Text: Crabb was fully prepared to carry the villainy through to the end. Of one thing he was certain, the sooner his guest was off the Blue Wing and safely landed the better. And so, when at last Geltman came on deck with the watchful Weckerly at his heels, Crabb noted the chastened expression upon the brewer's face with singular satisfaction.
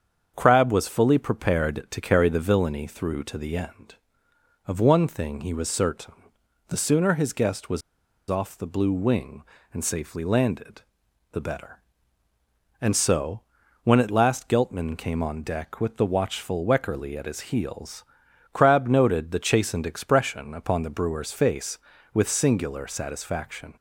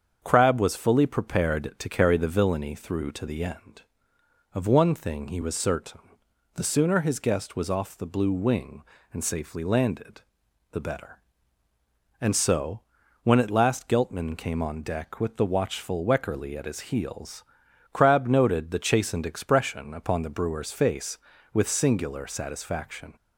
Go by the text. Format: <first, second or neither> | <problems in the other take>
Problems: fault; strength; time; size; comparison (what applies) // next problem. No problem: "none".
second | starts louder than the rest; strong; until 1.3 s; 7 dB; also in the second // pauses between "was" and "off"; noticeable; at 7.8 s; 0.48 s long // pauses between "landed" and "the"; noticeable; at 10.8 s; 0.50 s long; noticeable in the second